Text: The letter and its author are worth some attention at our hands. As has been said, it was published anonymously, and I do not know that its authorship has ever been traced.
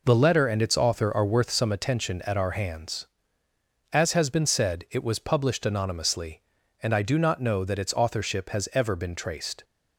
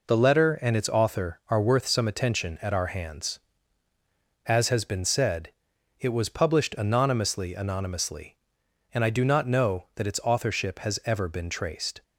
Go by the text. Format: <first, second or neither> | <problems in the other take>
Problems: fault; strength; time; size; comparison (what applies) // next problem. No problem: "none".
first | says "anonymously" twice; at 7.5 s